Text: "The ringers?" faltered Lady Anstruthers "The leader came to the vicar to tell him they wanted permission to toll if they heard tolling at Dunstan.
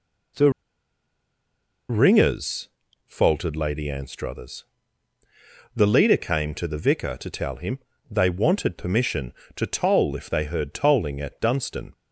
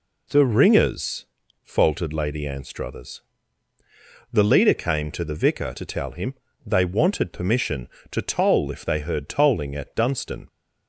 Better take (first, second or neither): second